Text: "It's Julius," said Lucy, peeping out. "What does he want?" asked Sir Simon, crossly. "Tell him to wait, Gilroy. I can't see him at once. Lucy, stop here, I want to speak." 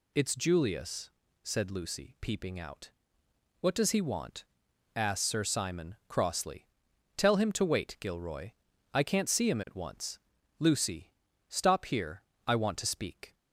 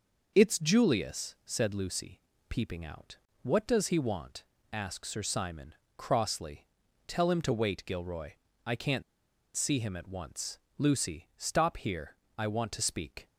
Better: first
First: none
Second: pauses between "can't" and "see"; noticeable; at 9.0 s; 0.53 s long

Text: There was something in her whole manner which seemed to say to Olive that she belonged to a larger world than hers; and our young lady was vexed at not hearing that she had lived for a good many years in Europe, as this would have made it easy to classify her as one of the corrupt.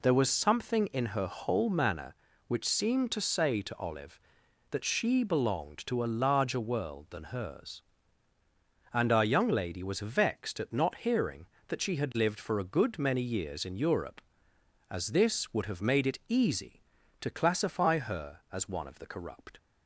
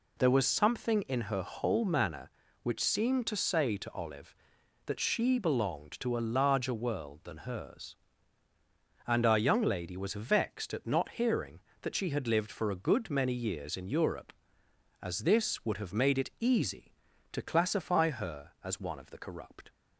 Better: neither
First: none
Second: none

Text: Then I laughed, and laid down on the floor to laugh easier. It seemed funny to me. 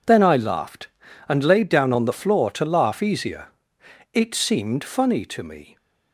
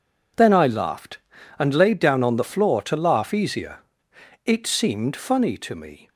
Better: neither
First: none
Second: none

